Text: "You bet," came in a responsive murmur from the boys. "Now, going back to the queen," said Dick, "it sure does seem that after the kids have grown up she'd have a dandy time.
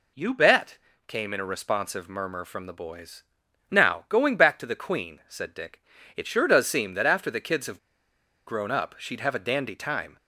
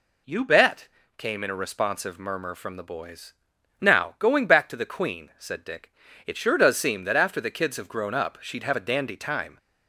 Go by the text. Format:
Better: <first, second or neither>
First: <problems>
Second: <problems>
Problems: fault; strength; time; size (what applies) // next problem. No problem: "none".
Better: second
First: pauses between "have" and "grown"; noticeable; at 7.7 s; 0.67 s long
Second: none